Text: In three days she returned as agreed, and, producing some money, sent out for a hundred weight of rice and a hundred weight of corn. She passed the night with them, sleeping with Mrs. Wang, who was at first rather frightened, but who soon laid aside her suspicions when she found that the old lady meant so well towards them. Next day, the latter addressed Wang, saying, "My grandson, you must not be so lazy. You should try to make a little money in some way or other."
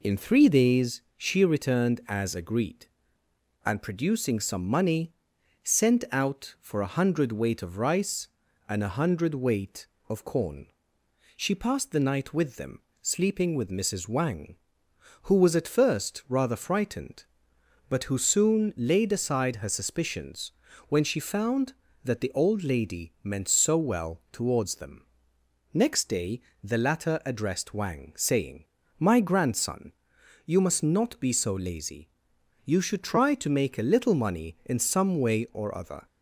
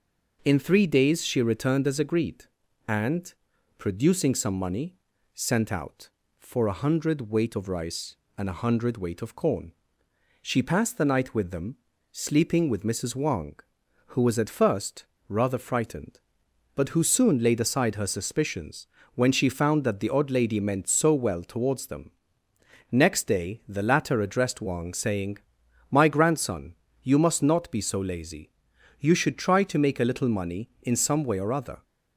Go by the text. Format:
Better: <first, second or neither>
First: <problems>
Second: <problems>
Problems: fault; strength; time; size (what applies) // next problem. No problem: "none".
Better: first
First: pauses between "suspicions" and "when"; slight; at 20.5 s; 0.36 s long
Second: pauses between "first" and "rather"; slight; at 15.0 s; 0.23 s long // pauses between "suspicions" and "when"; slight; at 18.8 s; 0.28 s long // says "odd" for "old"; at 20.0 s